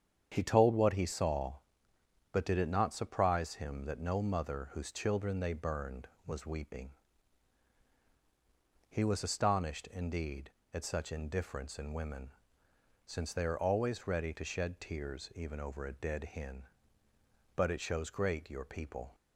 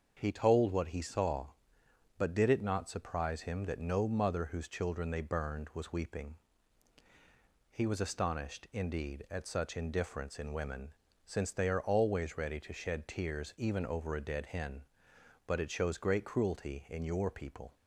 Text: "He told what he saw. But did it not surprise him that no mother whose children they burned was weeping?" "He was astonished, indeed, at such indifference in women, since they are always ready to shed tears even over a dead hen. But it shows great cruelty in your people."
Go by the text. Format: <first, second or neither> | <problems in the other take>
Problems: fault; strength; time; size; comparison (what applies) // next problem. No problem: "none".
second | starts louder than the rest; strong; until 1.3 s; 8 dB; also in the second // skips "cruelty in"; at 18.4 s